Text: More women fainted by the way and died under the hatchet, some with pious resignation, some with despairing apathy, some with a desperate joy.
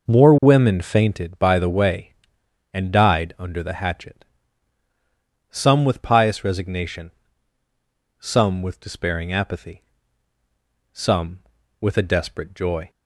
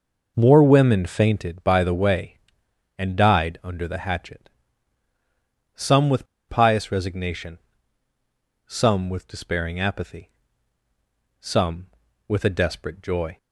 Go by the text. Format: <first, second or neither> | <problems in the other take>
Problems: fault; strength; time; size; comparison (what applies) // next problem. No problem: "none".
first | pauses between "with" and "pious"; slight; at 6.2 s; 0.22 s long